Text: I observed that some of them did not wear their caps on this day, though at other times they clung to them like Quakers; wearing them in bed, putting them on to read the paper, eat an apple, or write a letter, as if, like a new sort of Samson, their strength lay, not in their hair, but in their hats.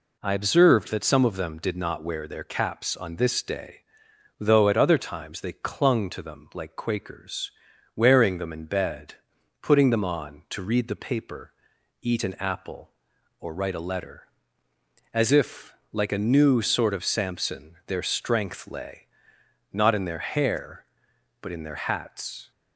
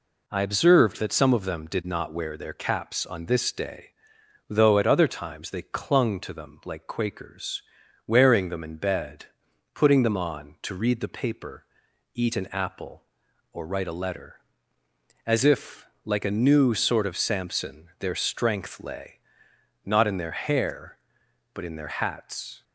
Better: neither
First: none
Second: none

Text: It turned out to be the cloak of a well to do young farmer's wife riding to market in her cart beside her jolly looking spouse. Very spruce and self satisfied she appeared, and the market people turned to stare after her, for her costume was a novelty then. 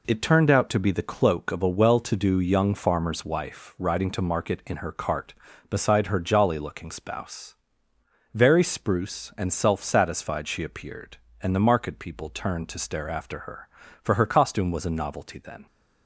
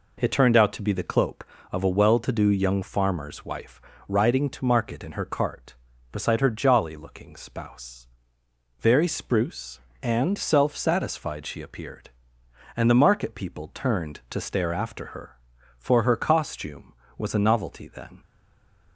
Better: first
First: none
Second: pauses between "wife" and "riding"; slight; at 3.8 s; 0.28 s long // stays silent after the last word; slight; from 18.2 s on; 0.7 s long

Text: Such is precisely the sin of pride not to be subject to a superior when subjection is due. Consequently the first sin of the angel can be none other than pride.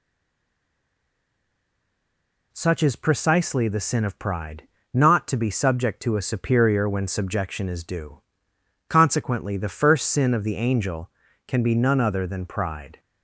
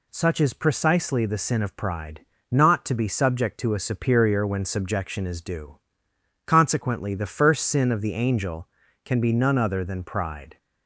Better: second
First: stays silent before the first word; strong; until 2.5 s; 2.5 s long // pauses between "pride" and "not"; slight; at 4.6 s; 0.26 s long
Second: pauses between "pride" and "not"; slight; at 2.2 s; 0.26 s long

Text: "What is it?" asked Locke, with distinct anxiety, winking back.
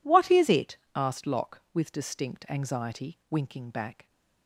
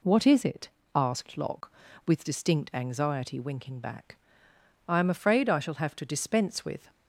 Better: first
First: none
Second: goes on to say "I am afraid I shall have to dispense with"; strong; from 4.8 s on; 2.0 s long

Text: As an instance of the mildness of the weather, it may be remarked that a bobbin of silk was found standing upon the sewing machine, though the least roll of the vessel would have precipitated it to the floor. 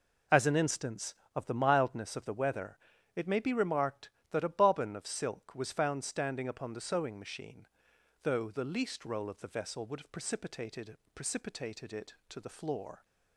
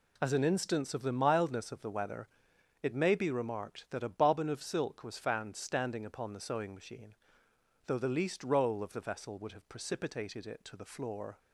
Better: second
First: says "precipitated" twice; at 11.1 s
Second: none

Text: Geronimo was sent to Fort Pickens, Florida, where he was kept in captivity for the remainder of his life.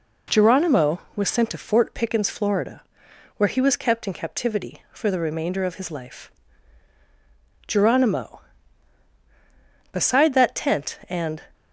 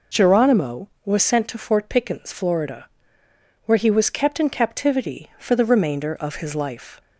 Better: second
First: goes on to say "GERONIMO Beside that tent and"; strong; from 7.6 s on; 3.7 s long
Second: none

